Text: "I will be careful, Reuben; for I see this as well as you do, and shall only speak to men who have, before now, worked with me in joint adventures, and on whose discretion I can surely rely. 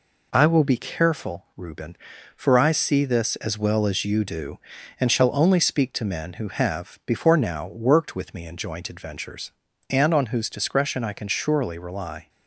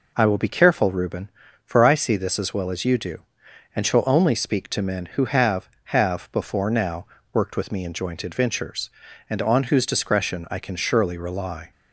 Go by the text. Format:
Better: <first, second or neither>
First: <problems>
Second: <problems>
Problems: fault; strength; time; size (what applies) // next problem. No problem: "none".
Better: first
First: none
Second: says "have" twice; at 5.8 s